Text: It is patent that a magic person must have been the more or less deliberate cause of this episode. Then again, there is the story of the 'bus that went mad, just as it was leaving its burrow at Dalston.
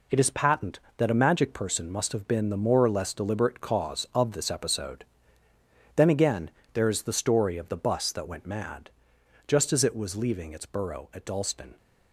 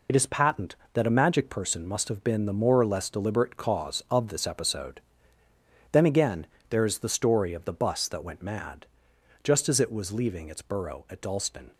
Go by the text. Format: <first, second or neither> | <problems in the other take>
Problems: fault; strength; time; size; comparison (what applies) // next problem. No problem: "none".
first | loses the start of "It"; at 0.0 s; 30 ms